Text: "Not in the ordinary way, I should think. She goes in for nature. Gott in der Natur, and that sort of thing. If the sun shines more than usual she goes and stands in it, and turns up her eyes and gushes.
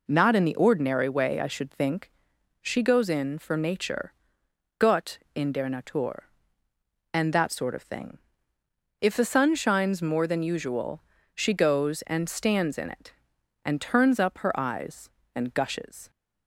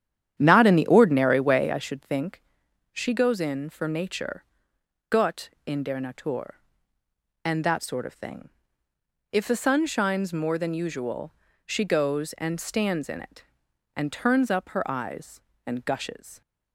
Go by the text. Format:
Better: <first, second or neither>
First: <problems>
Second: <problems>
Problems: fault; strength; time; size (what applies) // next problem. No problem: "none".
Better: first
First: pauses between "usual" and "she"; slight; at 10.9 s; 0.34 s long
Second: starts louder than the rest; strong; until 1.9 s; 10 dB // pauses between "usual" and "she"; slight; at 11.3 s; 0.34 s long